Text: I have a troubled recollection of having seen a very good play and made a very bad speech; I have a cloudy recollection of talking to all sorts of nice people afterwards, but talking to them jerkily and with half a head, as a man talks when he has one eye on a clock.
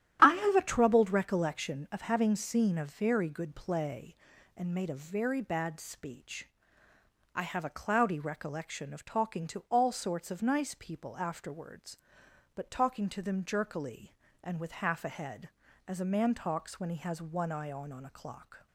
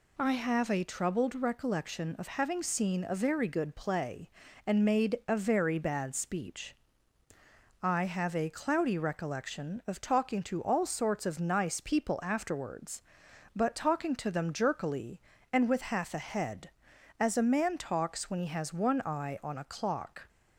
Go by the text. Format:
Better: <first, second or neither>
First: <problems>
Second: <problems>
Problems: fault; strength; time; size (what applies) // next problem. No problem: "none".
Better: second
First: starts louder than the rest; strong; until 1.2 s; 10.5 dB // says "on" twice; at 17.9 s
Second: none